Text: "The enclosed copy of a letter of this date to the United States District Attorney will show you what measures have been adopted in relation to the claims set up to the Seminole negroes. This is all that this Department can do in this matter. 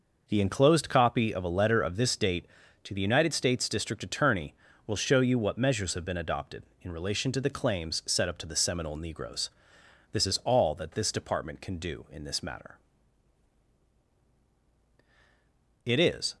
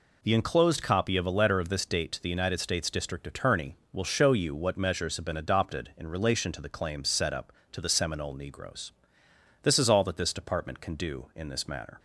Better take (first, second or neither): second